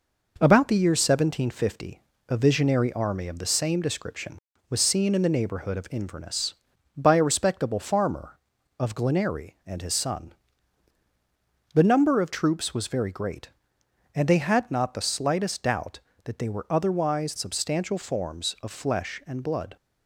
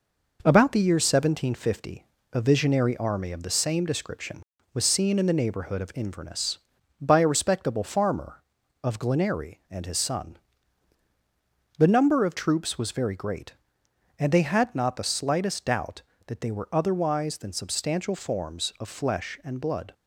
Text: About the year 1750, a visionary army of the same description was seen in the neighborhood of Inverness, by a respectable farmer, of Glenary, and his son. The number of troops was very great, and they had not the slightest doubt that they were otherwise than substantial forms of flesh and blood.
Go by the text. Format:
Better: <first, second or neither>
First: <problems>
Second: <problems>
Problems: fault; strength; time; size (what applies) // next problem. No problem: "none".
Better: second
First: skips "than"; at 17.3 s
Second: none